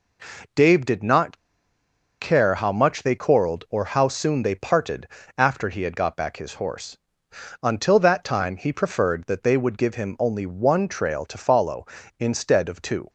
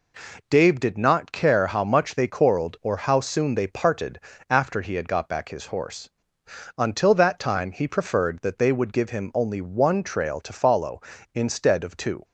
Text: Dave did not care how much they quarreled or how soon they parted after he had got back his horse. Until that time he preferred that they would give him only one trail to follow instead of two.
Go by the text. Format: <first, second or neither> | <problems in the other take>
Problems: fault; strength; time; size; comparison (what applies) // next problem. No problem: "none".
second | pauses between "not" and "care"; noticeable; at 1.3 s; 0.83 s long // pauses between "parted" and "after"; slight; at 5.0 s; 0.28 s long; slight in the second